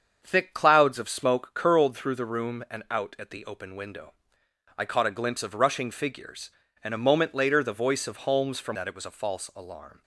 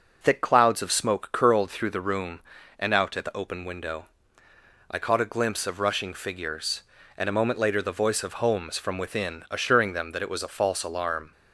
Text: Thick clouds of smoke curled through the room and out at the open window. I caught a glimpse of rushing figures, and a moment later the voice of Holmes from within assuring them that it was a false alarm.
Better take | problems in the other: second | starts louder than the rest; until 1.2 s; 7 dB // skips "within assuring them"; at 8.7 s

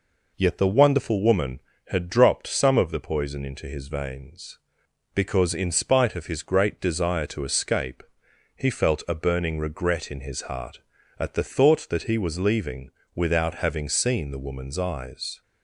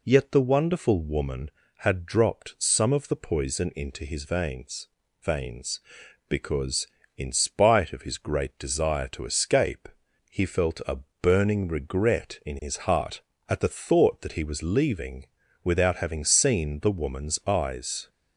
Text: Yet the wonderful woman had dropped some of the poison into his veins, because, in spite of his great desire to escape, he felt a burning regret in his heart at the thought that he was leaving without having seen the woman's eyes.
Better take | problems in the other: first | says "veins" twice; at 5.2 s // pauses between "a" and "burning"; slight; at 10.9 s; 0.24 s long // pauses between "leaving" and "without"; at 15.2 s; 0.38 s long; slight in the first

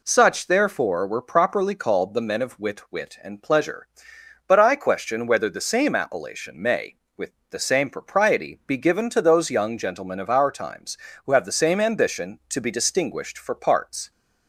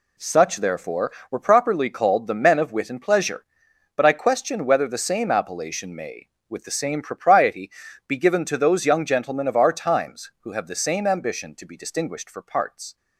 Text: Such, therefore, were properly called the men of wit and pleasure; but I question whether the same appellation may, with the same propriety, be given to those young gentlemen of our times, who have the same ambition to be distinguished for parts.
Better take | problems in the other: second | says "wit" twice; at 2.9 s // pauses between "with" and "the"; slight; at 7.3 s; 0.20 s long

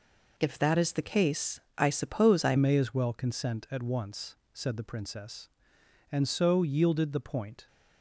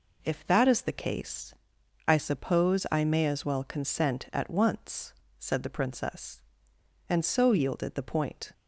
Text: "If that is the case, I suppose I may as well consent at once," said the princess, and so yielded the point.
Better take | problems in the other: second | changes voice at "may"; from 2.5 s on; 5.1 s long

